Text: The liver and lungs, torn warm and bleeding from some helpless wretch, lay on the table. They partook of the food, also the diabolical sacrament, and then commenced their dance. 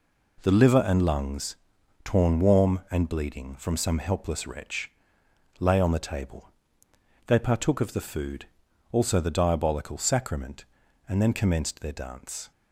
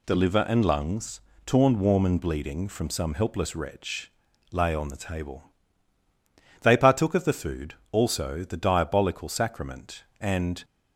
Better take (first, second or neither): first